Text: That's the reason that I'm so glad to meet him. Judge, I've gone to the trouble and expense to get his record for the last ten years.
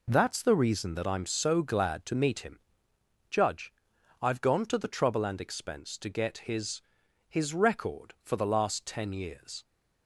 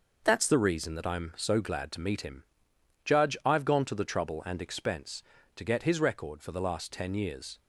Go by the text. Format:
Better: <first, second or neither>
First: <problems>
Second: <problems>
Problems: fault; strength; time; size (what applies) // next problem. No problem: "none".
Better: second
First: says "his" twice; at 7.2 s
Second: none